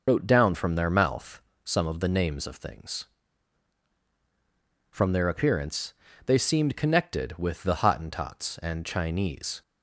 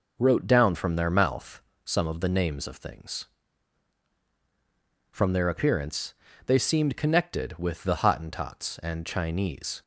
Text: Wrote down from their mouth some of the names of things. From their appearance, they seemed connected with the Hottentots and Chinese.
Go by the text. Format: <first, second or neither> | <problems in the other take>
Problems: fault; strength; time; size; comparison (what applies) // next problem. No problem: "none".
second | loses the start of "Wrote"; at 0.0 s; 90 ms // pauses between "mouth" and "some"; slight; at 1.4 s; 0.22 s long; slight in the second